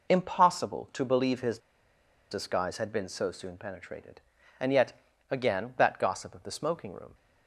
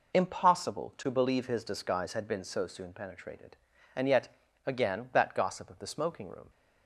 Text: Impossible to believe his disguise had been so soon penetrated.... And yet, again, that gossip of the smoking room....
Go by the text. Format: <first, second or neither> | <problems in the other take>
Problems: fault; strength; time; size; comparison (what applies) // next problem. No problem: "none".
second | pauses between "his" and "disguise"; noticeable; at 1.5 s; 0.72 s long